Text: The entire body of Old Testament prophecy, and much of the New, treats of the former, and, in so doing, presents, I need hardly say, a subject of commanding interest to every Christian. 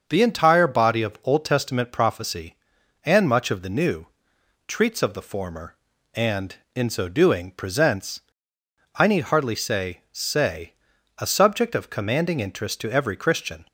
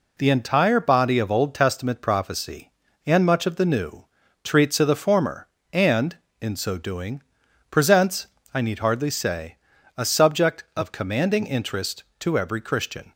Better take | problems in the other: second | starts louder than the rest; until 1.0 s; 6.5 dB // says "say" twice; at 10.1 s

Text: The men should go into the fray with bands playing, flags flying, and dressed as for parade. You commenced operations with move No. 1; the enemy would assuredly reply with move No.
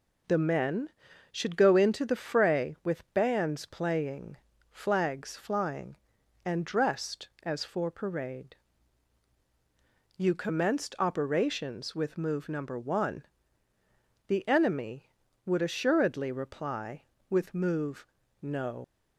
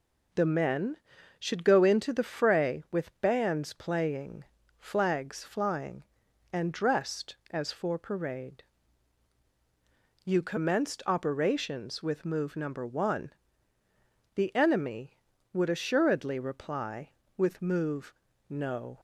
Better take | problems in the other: second | pauses between "move" and "No"; slight; at 18.0 s; 0.34 s long; slight in the second // leaves "No" unfinished; at 18.8 s; 80 ms

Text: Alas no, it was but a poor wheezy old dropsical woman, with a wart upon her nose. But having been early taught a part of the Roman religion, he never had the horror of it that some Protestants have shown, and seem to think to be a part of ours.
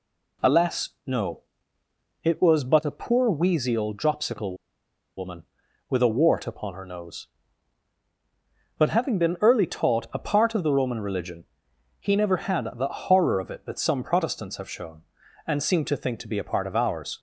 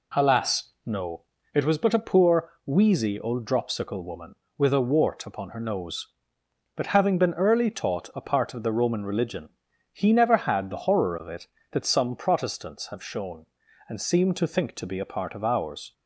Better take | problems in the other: second | pauses between "dropsical" and "woman"; noticeable; at 4.5 s; 0.62 s long

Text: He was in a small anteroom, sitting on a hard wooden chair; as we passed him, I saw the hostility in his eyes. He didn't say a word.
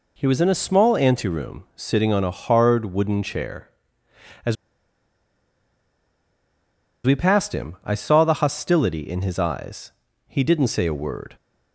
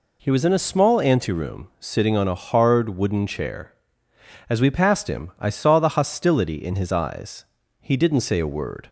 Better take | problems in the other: second | pauses between "as" and "we"; strong; at 4.5 s; 2.5 s long

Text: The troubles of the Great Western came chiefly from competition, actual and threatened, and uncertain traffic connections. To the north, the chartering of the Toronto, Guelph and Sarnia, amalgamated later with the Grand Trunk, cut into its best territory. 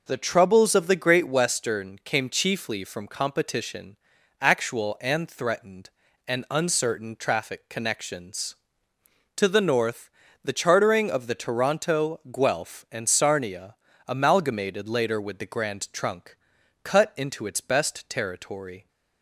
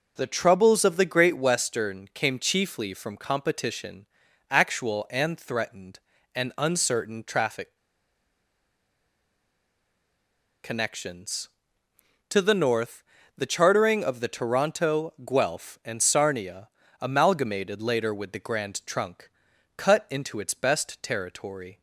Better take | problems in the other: first | pauses between "traffic" and "connections"; strong; at 7.7 s; 2.8 s long

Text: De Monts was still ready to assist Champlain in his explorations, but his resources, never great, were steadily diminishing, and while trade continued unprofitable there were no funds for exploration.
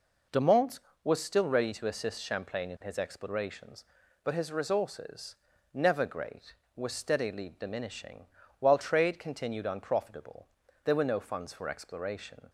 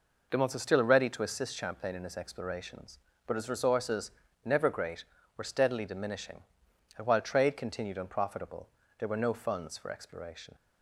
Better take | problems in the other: second | skips "and"; at 8.4 s // pauses between "unprofitable" and "there"; slight; at 10.4 s; 0.36 s long; slight in the second

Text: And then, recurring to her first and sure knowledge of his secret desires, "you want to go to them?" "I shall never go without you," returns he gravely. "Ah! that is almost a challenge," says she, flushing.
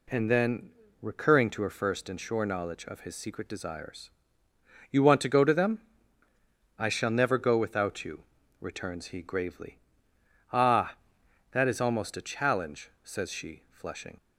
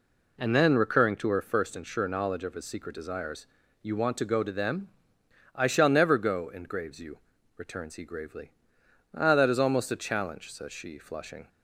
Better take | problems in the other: first | says "engraves" for "without"; at 6.4 s

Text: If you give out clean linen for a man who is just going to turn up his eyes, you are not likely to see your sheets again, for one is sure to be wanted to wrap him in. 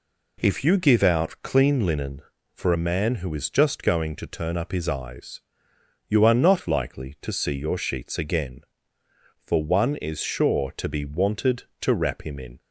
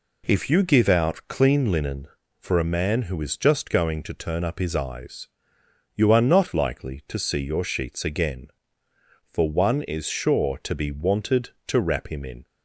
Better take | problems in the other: neither | none

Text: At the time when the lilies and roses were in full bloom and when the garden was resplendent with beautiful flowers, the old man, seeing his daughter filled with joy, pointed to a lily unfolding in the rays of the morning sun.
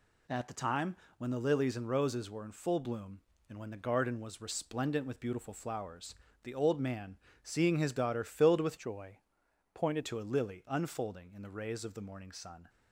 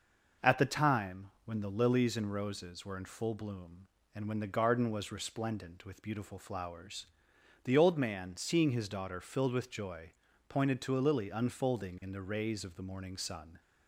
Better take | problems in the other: second | pauses between "time" and "when"; slight; at 0.9 s; 0.22 s long; slight in the second // changes voice from "joy" to "pointed"; from 8.7 to 10.0 s; 1.3 s long

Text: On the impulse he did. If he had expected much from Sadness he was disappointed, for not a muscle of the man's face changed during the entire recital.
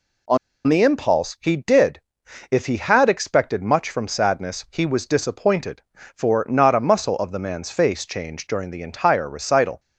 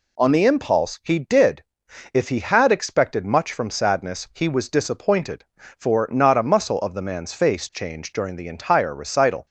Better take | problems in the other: second | pauses between "On" and "the"; slight; at 0.3 s; 0.30 s long

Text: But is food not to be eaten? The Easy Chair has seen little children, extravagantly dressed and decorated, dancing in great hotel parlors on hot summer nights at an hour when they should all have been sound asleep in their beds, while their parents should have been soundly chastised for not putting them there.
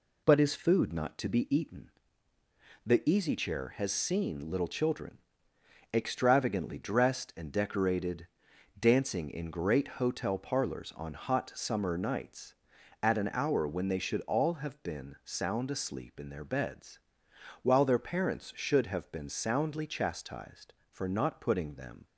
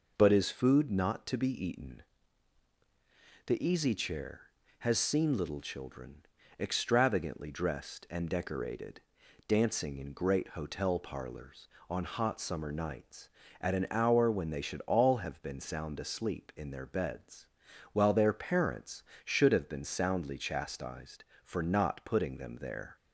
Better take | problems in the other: second | stops before "there"; at 22.0 s

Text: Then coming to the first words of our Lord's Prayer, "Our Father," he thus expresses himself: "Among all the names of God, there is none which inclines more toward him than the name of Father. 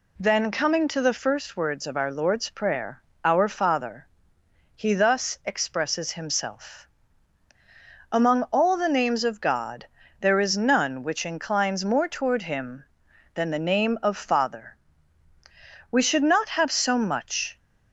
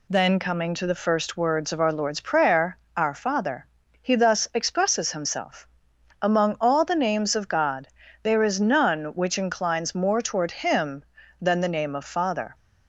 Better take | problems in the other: second | goes on to say "We should not have so much"; strong; from 15.9 s on; 1.6 s long

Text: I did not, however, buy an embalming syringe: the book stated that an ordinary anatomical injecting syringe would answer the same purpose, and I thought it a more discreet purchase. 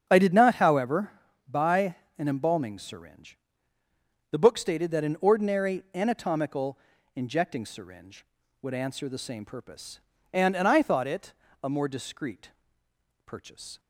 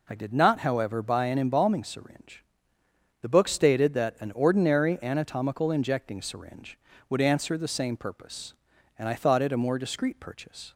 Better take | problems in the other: second | starts louder than the rest; strong; until 1.1 s; 7.5 dB // pauses between "buy" and "an"; slight; at 1.9 s; 0.22 s long // pauses between "anatomical" and "injecting"; slight; at 6.7 s; 0.36 s long // says "and" twice; at 10.5 s // pauses between "it" and "a"; slight; at 11.3 s; 0.28 s long // pauses between "discreet" and "purchase"; noticeable; at 12.5 s; 0.74 s long

